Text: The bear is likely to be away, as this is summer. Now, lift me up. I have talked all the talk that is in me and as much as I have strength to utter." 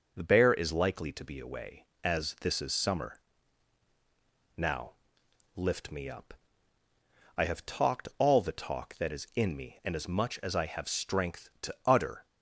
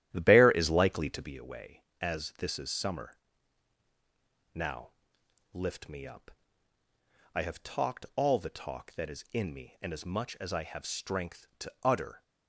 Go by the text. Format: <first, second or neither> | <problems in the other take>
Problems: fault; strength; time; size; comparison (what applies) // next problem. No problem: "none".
first | starts louder than the rest; strong; until 1.4 s; 11.5 dB